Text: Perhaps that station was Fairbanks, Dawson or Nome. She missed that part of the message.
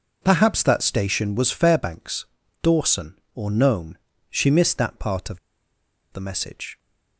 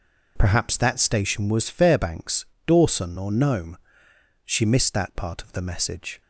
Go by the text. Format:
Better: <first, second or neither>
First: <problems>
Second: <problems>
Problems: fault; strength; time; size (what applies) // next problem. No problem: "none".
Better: second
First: pauses between "of" and "the"; noticeable; at 5.3 s; 0.73 s long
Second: none